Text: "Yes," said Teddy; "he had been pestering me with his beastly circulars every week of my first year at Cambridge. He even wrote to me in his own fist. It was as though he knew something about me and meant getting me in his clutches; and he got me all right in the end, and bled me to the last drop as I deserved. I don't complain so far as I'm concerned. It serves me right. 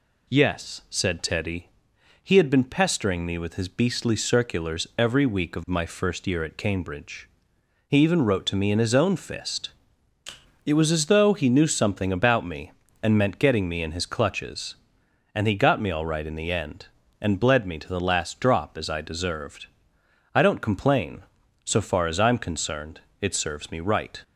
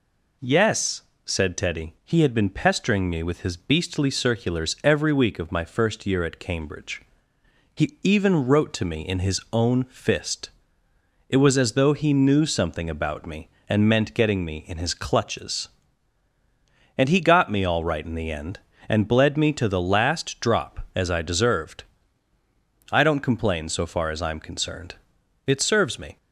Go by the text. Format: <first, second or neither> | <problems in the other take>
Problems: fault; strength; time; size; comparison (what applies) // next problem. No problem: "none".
first | stops before "right"; at 26.1 s